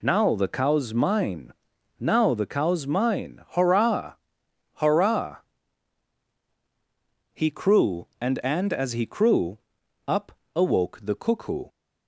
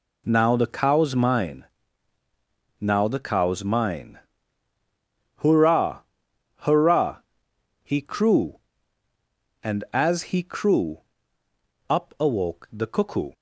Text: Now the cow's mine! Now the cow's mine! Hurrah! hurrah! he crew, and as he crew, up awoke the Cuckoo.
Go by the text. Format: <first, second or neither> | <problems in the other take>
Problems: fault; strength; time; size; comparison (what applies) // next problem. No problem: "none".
second | says "and" twice; at 8.4 s // pauses between "up" and "awoke"; slight; at 10.3 s; 0.22 s long